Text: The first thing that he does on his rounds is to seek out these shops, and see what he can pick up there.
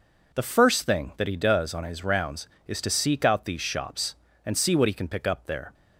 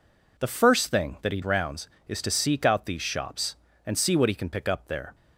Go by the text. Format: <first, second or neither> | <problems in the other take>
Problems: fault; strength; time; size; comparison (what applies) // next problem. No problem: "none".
first | skips "does on his"; at 1.4 s